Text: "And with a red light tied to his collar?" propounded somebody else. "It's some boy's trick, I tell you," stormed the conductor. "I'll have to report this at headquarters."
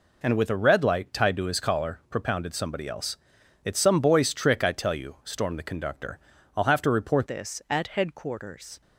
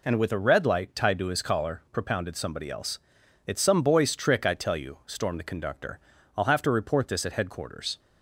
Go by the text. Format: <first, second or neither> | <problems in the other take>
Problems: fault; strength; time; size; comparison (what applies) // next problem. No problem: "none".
second | changes voice at "this"; from 7.2 s on; 1.6 s long